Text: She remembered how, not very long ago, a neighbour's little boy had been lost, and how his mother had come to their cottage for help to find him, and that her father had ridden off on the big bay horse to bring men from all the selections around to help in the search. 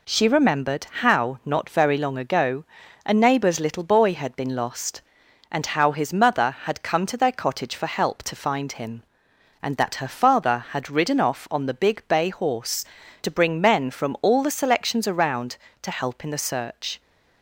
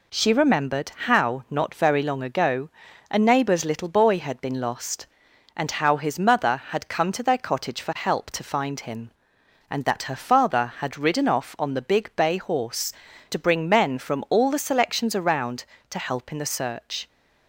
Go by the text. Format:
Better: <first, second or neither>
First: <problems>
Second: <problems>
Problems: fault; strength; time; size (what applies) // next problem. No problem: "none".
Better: neither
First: none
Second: none